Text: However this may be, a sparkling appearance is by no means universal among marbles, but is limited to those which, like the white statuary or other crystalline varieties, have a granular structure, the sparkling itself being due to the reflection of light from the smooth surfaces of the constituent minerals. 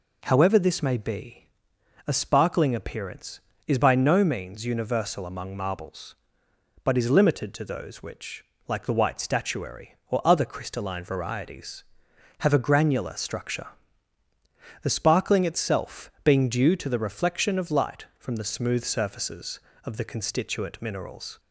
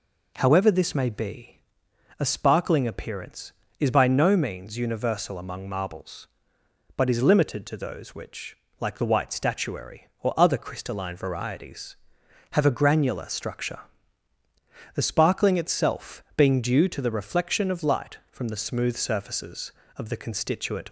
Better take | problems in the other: first | stops before "minerals"; at 20.8 s

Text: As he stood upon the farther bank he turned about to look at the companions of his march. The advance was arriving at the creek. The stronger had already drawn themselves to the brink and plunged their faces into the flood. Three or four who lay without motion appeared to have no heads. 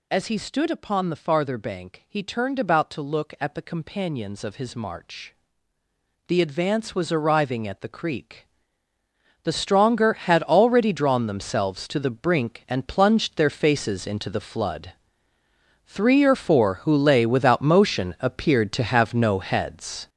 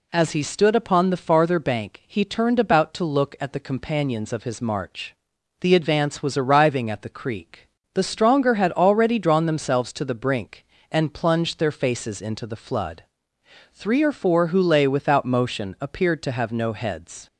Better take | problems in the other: second | gets louder; strong; throughout; 8.5 dB

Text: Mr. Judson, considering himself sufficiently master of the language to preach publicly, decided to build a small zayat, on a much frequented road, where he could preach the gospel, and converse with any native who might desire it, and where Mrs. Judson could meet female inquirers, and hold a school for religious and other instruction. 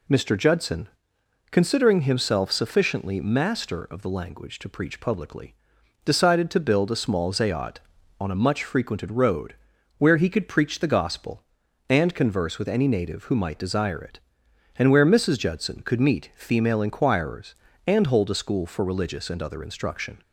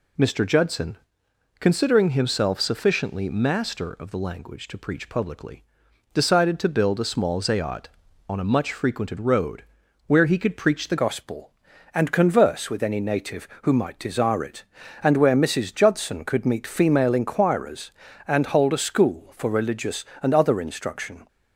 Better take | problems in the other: first | changes voice at "gospel"; from 10.9 s on; 10.3 s long

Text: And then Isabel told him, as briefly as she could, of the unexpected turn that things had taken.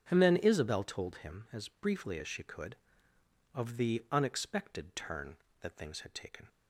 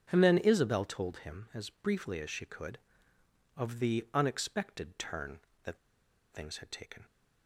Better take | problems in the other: first | starts louder than the rest; strong; until 1.1 s; 7.5 dB; strong in the first // pauses between "that" and "things"; noticeable; at 5.7 s; 0.54 s long

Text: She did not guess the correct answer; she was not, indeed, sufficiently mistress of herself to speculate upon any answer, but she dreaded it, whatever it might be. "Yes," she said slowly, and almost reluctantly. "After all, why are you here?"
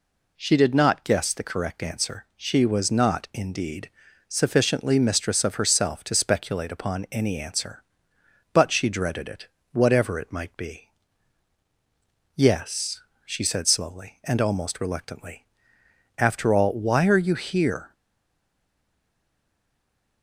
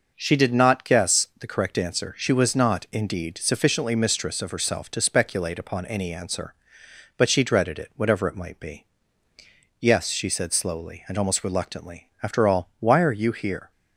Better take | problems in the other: second | stays silent after the last word; from 17.9 s on; 2.3 s long

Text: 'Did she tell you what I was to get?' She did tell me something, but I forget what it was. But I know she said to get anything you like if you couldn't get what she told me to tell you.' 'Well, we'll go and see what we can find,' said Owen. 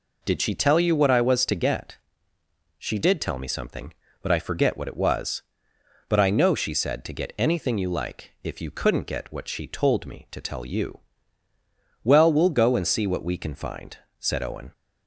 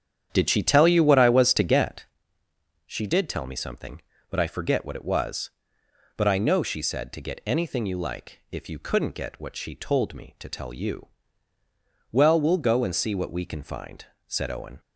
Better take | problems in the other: first | starts louder than the rest; strong; until 2.2 s; 9 dB

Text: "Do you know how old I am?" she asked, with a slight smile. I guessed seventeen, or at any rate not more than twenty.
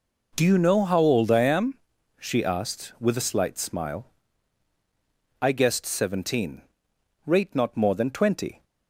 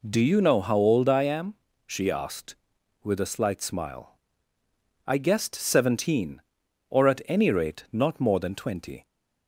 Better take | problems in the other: second | skips "or at any"; at 6.9 s

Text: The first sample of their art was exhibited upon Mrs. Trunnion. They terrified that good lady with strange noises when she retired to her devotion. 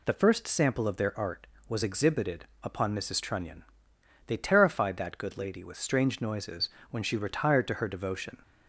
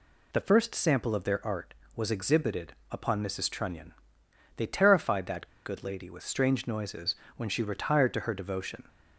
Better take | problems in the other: first | pauses between "exhibited" and "upon"; slight; at 2.7 s; 0.18 s long; slight in the first // pauses between "that" and "good"; slight; at 5.4 s; 0.18 s long // pauses between "noises" and "when"; slight; at 7.1 s; 0.22 s long; slight in the first

